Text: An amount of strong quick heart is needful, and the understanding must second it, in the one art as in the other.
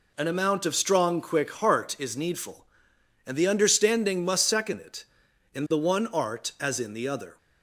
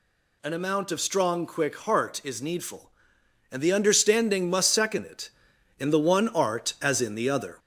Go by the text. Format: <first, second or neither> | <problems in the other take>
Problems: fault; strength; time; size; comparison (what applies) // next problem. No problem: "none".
first | gets louder; slight; throughout; 2 dB